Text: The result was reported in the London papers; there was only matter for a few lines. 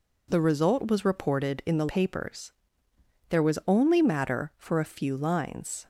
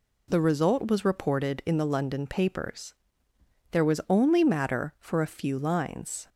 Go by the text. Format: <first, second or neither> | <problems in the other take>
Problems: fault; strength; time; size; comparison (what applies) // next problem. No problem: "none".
second | skips "London"; at 1.8 s